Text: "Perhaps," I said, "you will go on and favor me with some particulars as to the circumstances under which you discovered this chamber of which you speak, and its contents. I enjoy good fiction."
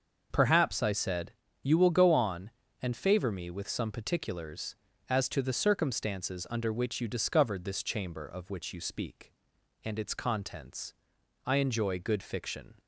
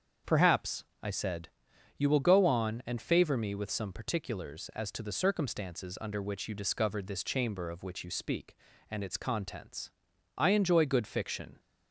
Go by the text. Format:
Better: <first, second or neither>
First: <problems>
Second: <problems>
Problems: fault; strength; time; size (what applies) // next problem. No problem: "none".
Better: neither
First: starts louder than the rest; until 1.3 s; 6.5 dB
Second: starts louder than the rest; until 1.4 s; 7 dB